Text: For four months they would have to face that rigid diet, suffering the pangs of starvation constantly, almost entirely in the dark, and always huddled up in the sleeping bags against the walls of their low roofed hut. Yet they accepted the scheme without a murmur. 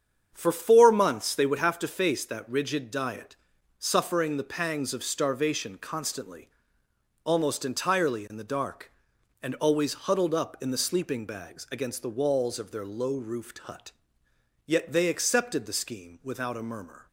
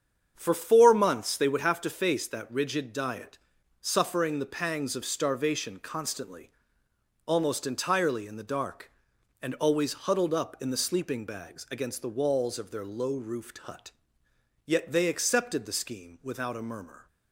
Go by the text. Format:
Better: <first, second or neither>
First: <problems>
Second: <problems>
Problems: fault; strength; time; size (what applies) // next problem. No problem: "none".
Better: neither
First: starts louder than the rest; strong; until 1.3 s; 8 dB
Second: starts louder than the rest; strong; until 1.3 s; 8 dB